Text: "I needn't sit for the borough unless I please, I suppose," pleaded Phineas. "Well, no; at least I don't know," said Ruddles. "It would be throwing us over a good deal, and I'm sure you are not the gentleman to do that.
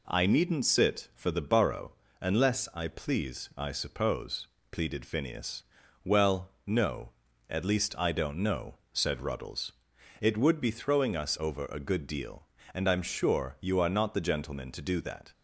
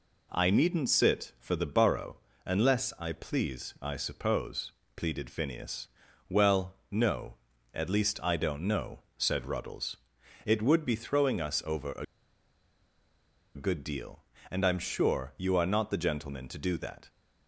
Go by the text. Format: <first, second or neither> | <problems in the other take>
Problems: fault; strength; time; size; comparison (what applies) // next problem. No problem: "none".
first | pauses between "borough" and "unless"; slight; at 2.1 s; 0.26 s long; slight in the first // pauses between "a" and "good"; strong; at 12.0 s; 1.5 s long